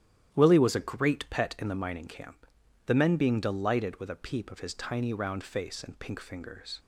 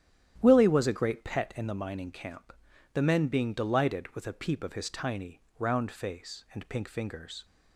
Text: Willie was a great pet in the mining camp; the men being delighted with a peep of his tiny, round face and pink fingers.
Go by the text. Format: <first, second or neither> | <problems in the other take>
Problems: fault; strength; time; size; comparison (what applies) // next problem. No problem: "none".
neither | starts louder than the rest; strong; the same in both